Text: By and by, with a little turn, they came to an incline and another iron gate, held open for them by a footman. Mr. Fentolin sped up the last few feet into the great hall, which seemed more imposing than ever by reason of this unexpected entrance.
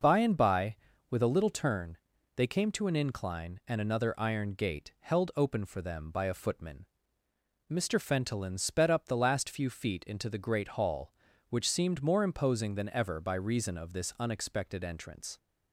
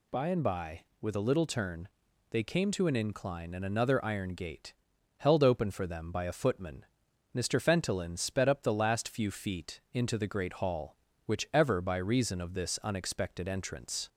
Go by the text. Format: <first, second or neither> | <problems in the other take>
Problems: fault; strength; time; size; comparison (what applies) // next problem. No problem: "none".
first | skips "seemed more imposing than"; at 11.5 s